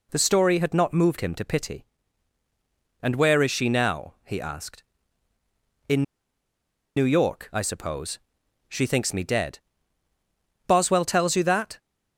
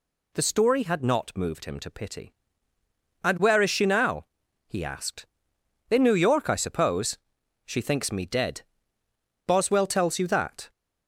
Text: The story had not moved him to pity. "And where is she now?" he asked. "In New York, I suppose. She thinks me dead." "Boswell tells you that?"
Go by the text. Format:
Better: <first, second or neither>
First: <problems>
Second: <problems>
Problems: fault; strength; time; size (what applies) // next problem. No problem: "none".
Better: second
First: pauses between "In" and "New"; noticeable; at 6.0 s; 0.93 s long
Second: none